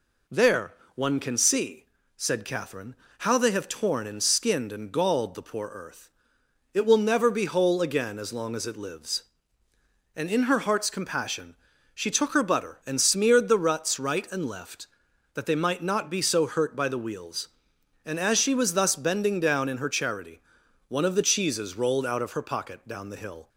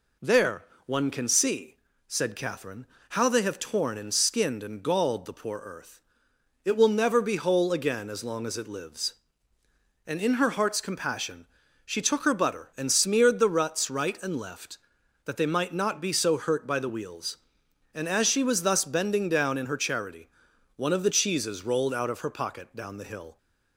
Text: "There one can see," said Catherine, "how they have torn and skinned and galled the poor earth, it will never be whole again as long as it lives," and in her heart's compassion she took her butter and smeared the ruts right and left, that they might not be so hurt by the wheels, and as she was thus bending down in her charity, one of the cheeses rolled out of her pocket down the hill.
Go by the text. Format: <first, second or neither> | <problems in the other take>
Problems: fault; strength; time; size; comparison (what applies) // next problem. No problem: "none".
neither | pauses between "There" and "one"; slight; the same in both // pauses between "compassion" and "she"; the same in both